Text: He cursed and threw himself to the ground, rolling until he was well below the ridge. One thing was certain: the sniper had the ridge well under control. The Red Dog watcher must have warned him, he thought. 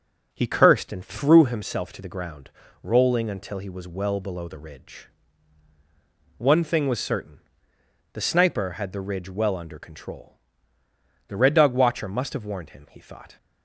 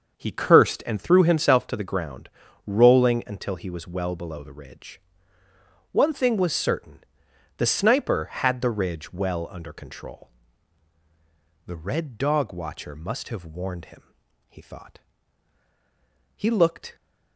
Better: first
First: none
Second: starts louder than the rest; until 1.1 s; 6.5 dB // goes on to say "He looked"; from 16.3 s on; 0.58 s long

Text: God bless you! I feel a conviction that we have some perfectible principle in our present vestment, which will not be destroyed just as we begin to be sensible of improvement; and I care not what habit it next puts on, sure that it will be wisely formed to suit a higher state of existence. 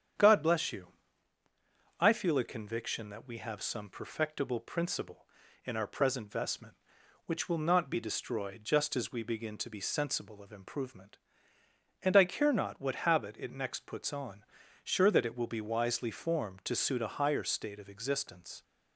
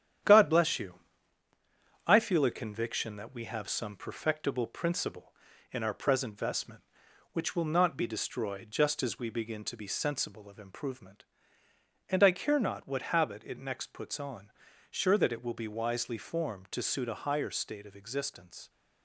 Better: first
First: starts louder than the rest; strong; until 2.3 s; 8.5 dB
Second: gets quieter; noticeable; throughout; 5.5 dB // starts louder than the rest; strong; until 2.4 s; 10 dB

